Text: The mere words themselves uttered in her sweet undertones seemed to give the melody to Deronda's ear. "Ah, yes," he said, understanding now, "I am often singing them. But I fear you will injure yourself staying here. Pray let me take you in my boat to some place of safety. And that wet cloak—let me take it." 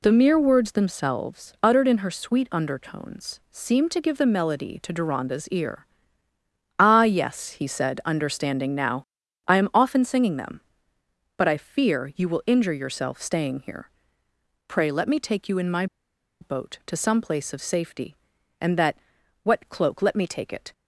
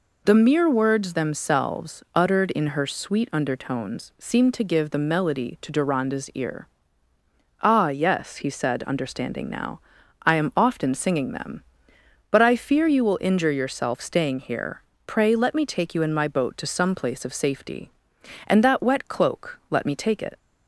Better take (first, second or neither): second